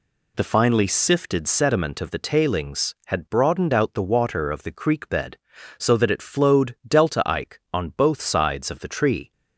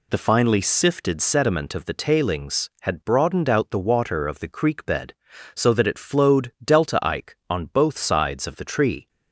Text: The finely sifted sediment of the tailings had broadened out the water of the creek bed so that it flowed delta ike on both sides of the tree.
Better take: neither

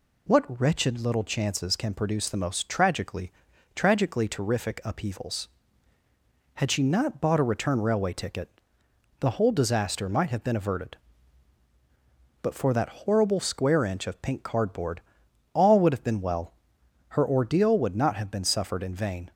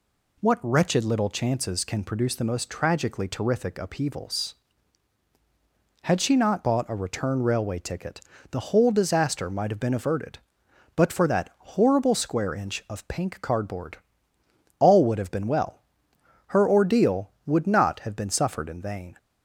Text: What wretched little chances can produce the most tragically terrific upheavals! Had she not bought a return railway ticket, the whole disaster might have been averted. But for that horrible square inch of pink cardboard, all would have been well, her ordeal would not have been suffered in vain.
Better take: second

